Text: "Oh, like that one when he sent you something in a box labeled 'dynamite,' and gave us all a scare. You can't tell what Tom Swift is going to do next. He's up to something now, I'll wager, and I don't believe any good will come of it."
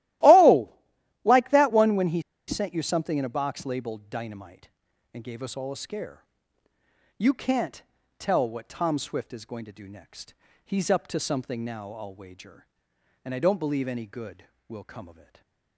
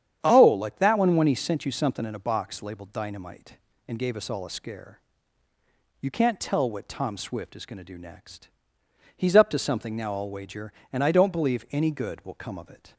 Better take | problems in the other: second | starts louder than the rest; strong; until 1.7 s; 15 dB; strong in the second // pauses between "he" and "sent"; slight; at 2.2 s; 0.26 s long // pauses between "can't" and "tell"; slight; at 7.8 s; 0.34 s long // stays silent after the last word; slight; from 15.1 s on; 0.6 s long

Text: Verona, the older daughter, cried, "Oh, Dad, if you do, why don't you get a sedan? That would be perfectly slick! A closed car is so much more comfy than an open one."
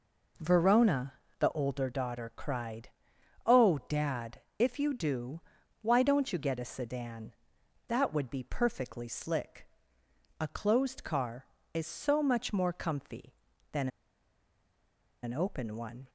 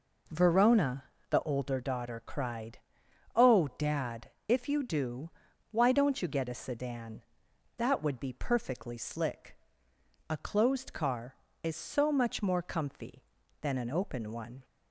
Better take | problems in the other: second | pauses between "than" and "an"; strong; at 13.8 s; 1.3 s long

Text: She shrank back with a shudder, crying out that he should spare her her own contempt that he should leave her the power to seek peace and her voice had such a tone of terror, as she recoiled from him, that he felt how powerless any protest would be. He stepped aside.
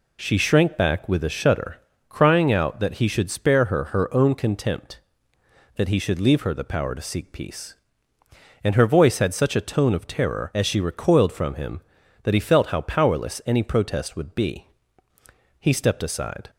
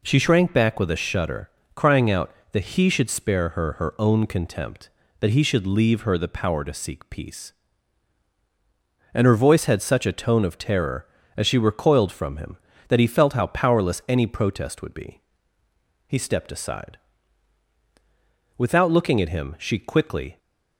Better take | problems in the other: first | goes on to say "Without looking at him she quickly"; strong; from 18.5 s on; 1.8 s long

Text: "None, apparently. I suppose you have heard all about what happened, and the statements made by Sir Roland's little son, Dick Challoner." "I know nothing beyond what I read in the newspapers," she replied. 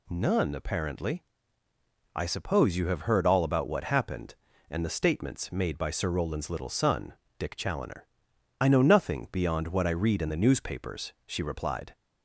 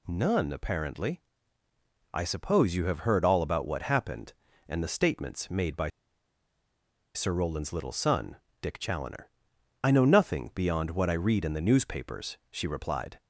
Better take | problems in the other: first | pauses between "by" and "Sir"; strong; at 5.8 s; 1.2 s long

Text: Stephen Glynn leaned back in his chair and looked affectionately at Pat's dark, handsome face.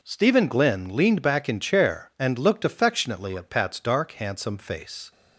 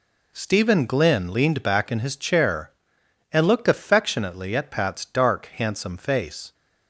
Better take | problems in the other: second | skips "his"; at 1.5 s

